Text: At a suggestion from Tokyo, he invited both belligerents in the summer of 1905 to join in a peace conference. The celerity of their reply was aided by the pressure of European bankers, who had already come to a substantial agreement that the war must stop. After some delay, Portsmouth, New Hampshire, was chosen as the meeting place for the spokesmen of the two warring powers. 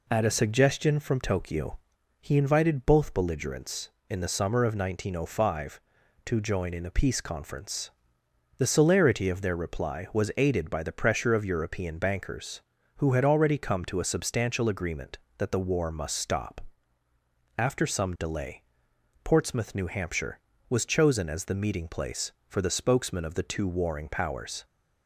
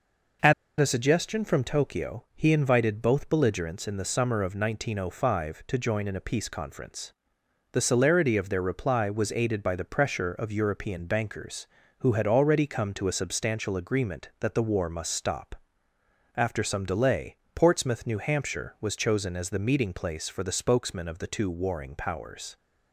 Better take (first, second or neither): first